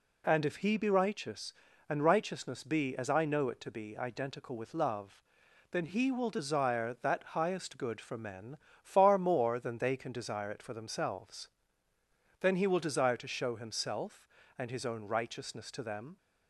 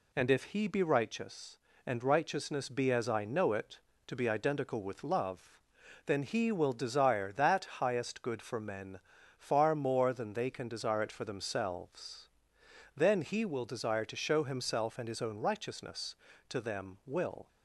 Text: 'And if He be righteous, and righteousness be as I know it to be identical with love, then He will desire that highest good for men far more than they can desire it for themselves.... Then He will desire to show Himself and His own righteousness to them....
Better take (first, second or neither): first